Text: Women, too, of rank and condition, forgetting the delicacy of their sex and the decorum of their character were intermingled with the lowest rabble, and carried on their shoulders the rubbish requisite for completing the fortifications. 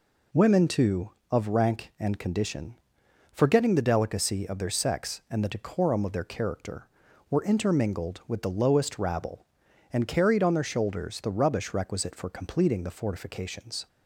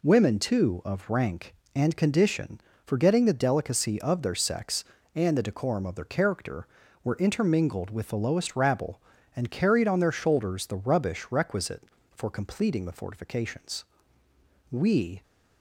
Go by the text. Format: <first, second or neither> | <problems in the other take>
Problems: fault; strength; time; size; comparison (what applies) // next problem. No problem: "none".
first | goes on to say "We"; from 14.7 s on; 0.52 s long